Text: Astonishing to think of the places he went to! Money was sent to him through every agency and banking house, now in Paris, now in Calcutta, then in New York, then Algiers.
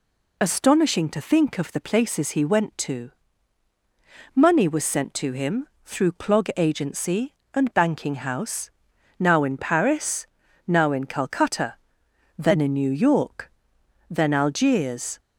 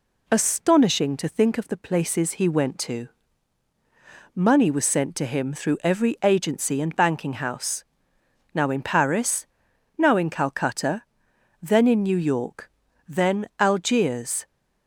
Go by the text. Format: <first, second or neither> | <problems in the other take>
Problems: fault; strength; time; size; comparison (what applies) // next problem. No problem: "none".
second | pauses between "him" and "through"; slight; at 5.6 s; 0.16 s long // says "clog" for "every"; at 6.1 s